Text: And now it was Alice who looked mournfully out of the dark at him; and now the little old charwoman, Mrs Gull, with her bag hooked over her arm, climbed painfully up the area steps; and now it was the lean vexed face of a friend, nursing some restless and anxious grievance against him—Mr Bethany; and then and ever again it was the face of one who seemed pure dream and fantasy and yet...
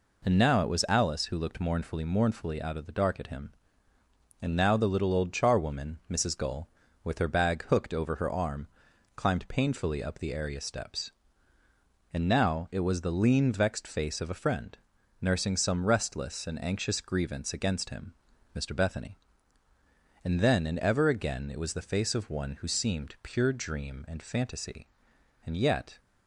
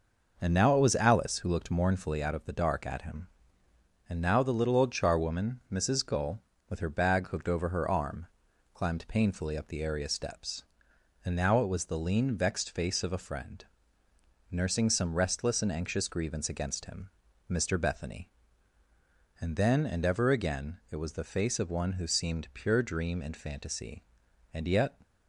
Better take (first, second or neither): second